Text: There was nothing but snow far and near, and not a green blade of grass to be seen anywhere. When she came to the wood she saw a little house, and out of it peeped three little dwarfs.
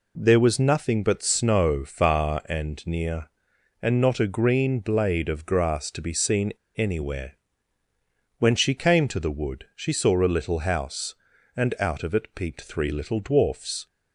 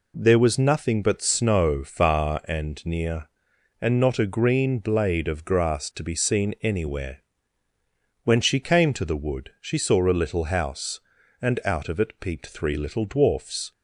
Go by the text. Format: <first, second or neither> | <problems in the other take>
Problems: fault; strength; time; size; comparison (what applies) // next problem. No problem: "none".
second | pauses between "seen" and "anywhere"; slight; at 6.5 s; 0.20 s long